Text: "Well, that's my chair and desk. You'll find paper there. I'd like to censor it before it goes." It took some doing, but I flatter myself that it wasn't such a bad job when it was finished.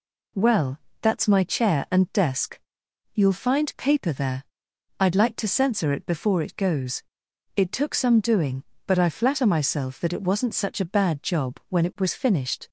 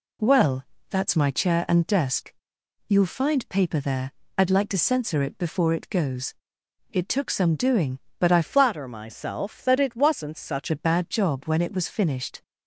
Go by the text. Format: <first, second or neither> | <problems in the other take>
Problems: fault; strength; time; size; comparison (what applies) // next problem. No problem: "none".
first | changes voice from "flatter" to "such"; from 8.4 to 10.7 s; 2.3 s long